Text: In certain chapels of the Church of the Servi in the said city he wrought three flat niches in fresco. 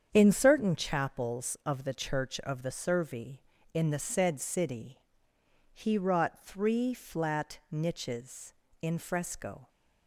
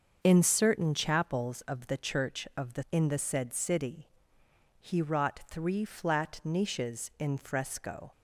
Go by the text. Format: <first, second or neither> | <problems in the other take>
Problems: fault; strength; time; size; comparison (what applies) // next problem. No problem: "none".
first | starts louder than the rest; until 1.2 s; 6.5 dB; strong in the first // skips "Servi"; at 2.8 s // pauses between "city" and "he"; noticeable; at 4.0 s; 0.72 s long; noticeable in the first